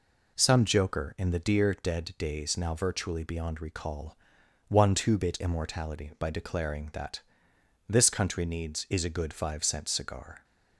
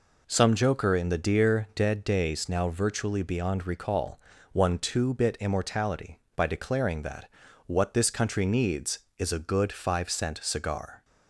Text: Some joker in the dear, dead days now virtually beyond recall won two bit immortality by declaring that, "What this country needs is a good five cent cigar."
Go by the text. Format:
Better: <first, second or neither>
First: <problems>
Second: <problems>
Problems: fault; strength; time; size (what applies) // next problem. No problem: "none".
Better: second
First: pauses between "recall" and "won"; noticeable; at 4.1 s; 0.50 s long // skips "What"; at 7.5 s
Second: pauses between "recall" and "won"; slight; at 4.1 s; 0.36 s long